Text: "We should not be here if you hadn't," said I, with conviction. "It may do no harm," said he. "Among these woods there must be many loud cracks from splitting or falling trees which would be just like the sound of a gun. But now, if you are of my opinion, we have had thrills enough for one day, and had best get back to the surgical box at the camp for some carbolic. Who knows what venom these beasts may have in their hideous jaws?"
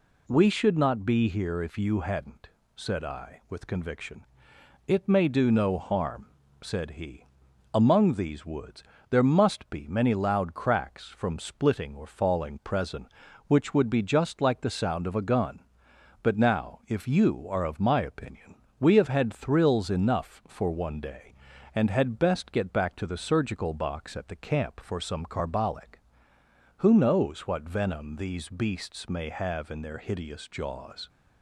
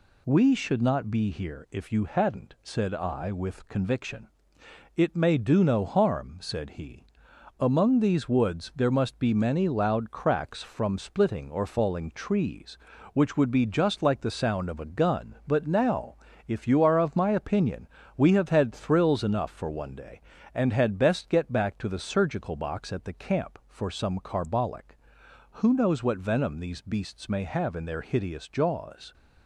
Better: second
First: pauses between "woods" and "there"; slight; at 8.8 s; 0.28 s long // says "presen" for "trees"; at 12.6 s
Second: none

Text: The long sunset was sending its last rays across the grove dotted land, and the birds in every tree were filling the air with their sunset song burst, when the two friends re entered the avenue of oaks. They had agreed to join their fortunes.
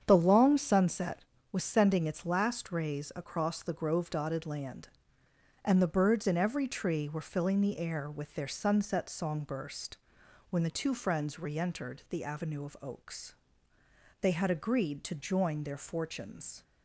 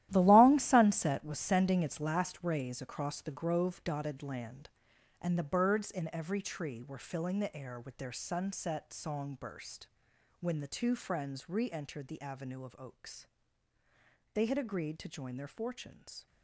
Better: first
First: starts louder than the rest; strong; until 1.0 s; 8 dB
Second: gets quieter; strong; throughout; 12.5 dB // starts louder than the rest; strong; until 1.1 s; 13.5 dB

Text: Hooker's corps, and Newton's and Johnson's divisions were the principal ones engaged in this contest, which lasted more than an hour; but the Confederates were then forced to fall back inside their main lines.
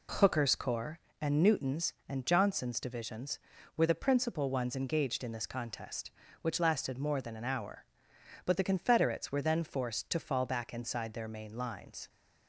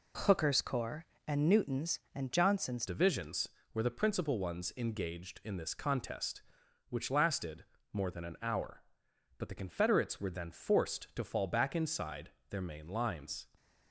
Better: first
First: none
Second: changes voice at "divisions"; from 2.8 s on; 10.6 s long // pauses between "lasted" and "more"; slight; at 7.6 s; 0.28 s long // pauses between "inside" and "their"; slight; at 12.2 s; 0.20 s long

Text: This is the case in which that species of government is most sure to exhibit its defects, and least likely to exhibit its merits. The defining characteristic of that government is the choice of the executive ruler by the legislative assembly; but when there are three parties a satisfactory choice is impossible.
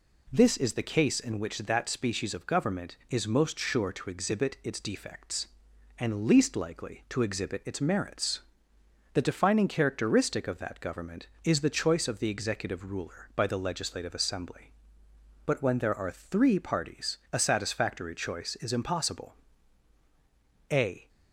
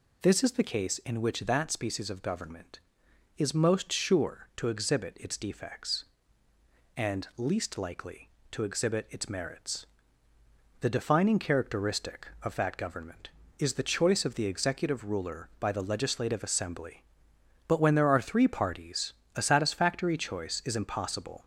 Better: second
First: pauses between "parties" and "a"; slight; at 17.1 s; 0.16 s long // goes on to say "A"; slight; from 20.6 s on; 0.38 s long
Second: pauses between "parties" and "a"; slight; at 19.1 s; 0.24 s long

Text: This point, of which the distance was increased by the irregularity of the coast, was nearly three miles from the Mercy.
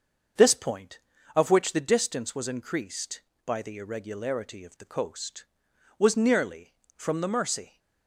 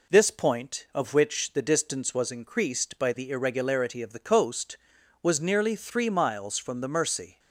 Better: second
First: starts louder than the rest; until 1.7 s; 6.5 dB // skips "three miles"; at 6.8 s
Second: none

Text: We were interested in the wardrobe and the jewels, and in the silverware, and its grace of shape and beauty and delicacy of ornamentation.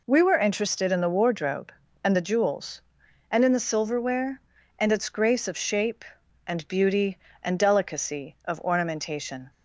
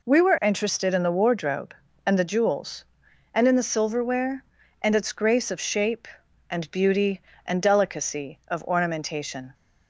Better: neither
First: none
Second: none

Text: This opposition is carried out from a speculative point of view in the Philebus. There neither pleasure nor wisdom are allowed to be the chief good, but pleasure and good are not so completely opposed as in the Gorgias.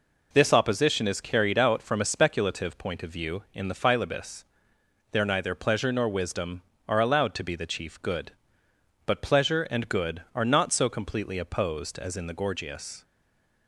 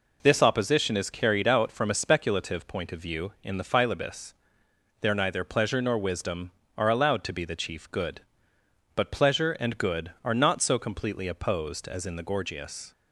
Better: second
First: stays silent after the last word; slight; from 13.0 s on; 0.6 s long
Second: none

